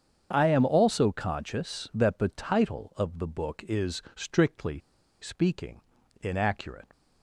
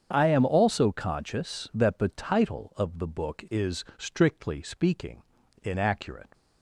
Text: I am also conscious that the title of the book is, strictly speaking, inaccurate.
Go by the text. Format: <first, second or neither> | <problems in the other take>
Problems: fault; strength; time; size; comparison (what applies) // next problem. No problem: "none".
second | starts louder than the rest; strong; until 1.3 s; 7.5 dB; strong in the second // pauses between "strictly" and "speaking"; at 4.7 s; 0.41 s long